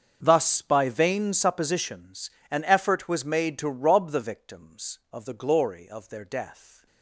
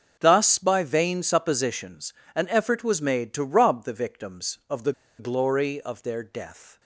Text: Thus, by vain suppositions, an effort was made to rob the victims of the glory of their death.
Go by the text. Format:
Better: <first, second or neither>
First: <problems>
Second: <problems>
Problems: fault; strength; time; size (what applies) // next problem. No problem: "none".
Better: first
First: starts louder than the rest; until 1.2 s; 6.5 dB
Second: starts louder than the rest; until 1.2 s; 6.5 dB // pauses between "the" and "glory"; slight; at 4.9 s; 0.25 s long